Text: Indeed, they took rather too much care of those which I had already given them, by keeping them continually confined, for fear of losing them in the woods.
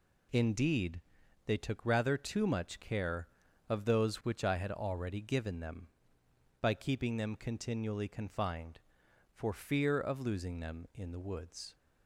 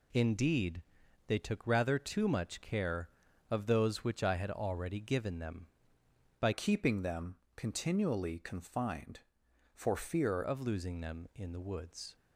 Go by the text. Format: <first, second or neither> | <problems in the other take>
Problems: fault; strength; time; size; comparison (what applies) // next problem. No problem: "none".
first | changes voice from "keeping" to "fear"; from 6.5 to 10.4 s; 3.9 s long // pauses between "them" and "continually"; slight; at 7.3 s; 0.18 s long